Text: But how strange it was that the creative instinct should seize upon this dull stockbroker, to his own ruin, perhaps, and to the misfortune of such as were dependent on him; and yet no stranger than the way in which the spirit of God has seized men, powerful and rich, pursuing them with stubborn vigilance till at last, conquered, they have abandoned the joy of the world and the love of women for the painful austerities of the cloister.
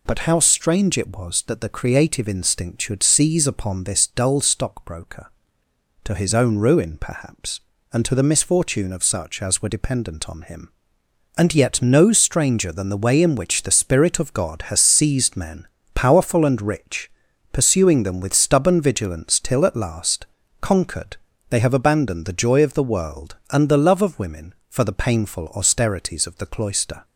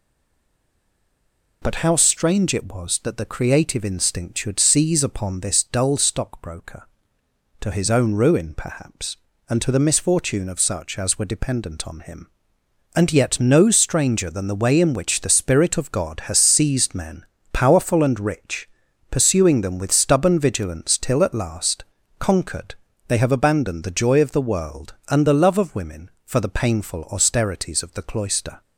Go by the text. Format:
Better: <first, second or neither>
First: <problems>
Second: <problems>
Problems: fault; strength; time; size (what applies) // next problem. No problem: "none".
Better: first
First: none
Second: stays silent before the first word; noticeable; until 1.6 s; 1.6 s long